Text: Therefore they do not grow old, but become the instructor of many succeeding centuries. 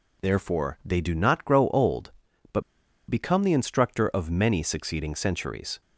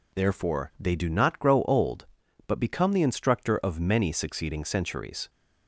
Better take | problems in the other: second | pauses between "but" and "become"; noticeable; at 2.6 s; 0.47 s long

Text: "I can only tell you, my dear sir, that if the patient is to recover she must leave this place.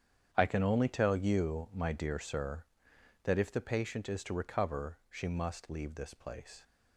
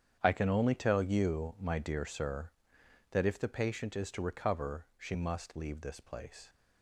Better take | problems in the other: neither | starts louder than the rest; strong; the same in both

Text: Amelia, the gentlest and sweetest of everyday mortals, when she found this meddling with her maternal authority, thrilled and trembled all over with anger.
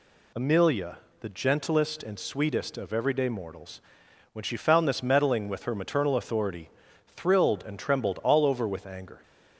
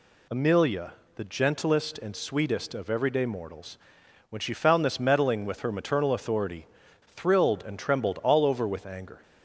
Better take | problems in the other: neither | none

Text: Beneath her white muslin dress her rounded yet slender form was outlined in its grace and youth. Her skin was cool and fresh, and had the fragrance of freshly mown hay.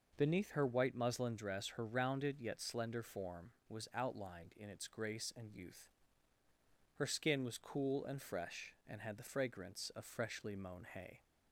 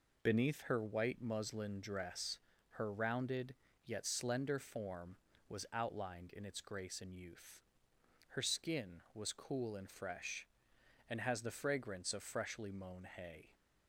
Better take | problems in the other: first | pauses between "dress" and "her"; slight; at 2.3 s; 0.32 s long // pauses between "rounded" and "yet"; slight; at 3.5 s; 0.30 s long // says "has" for "had"; at 11.2 s

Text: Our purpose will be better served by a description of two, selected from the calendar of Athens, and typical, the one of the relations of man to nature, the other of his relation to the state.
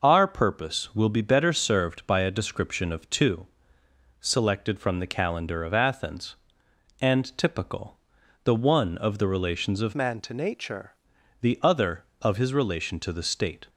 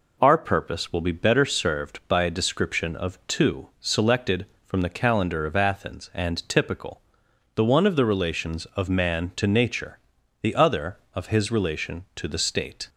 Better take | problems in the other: second | changes voice from "man" to "nature"; from 9.9 to 10.9 s; 1.0 s long

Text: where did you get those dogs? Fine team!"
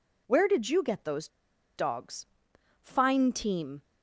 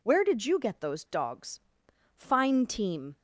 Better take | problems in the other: second | pauses between "those" and "dogs"; noticeable; at 1.2 s; 0.49 s long

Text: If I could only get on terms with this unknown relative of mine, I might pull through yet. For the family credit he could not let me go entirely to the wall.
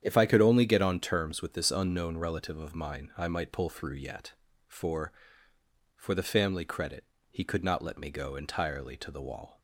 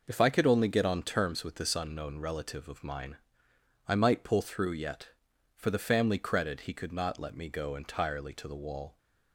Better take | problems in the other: second | starts louder than the rest; strong; until 1.0 s; 9 dB // says "For" twice; at 5.9 s // pauses between "credit" and "he"; slight; at 7.0 s; 0.26 s long

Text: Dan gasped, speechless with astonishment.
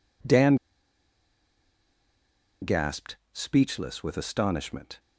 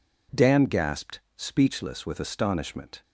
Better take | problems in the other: second | pauses between "Dan" and "gasped"; strong; at 0.5 s; 2.0 s long

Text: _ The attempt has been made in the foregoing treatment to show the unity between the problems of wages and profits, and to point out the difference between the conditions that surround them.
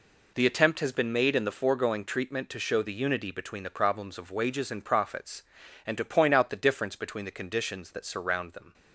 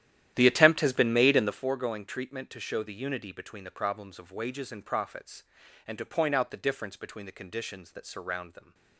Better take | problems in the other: first | starts louder than the rest; strong; until 1.7 s; 11.5 dB

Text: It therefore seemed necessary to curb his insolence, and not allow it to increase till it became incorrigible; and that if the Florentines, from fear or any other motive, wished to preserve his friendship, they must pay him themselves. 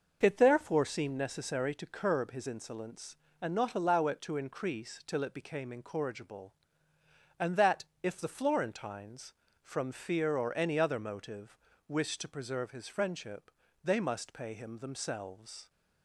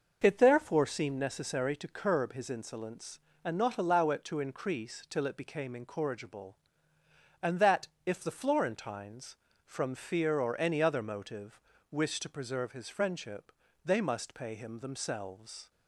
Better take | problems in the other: neither | pauses between "that" and "if"; slight; the same in both

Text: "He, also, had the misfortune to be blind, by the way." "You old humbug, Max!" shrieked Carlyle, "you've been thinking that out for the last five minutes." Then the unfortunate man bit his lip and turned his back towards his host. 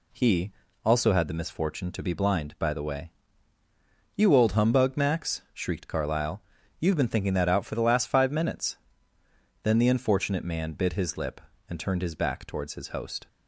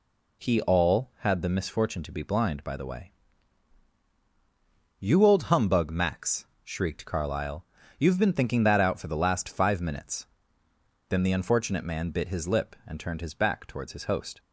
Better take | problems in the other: first | says "all" for "also"; at 0.6 s

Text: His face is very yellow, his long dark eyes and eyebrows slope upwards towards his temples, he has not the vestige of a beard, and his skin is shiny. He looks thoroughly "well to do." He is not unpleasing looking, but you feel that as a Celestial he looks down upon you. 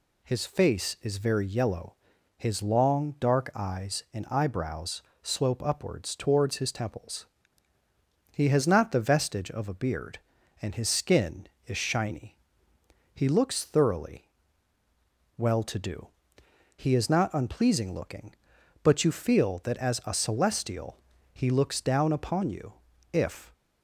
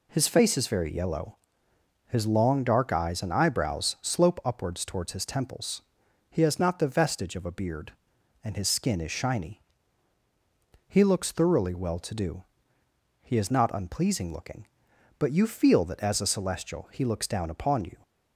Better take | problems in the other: second | pauses between "eyebrows" and "slope"; slight; at 5.0 s; 0.20 s long // pauses between "thoroughly" and "well"; at 14.2 s; 1.1 s long // pauses between "Celestial" and "he"; slight; at 20.9 s; 0.36 s long // goes on to say "If"; slight; from 23.1 s on; 0.40 s long

